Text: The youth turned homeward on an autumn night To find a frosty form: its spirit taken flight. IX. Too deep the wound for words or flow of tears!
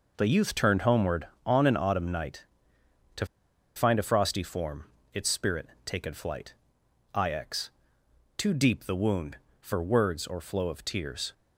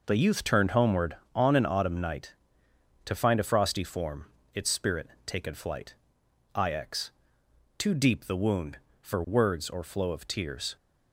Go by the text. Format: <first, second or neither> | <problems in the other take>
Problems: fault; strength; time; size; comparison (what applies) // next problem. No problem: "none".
second | pauses between "To" and "find"; noticeable; at 3.2 s; 0.51 s long // pauses between "spirit" and "taken"; slight; at 5.6 s; 0.20 s long; slight in the second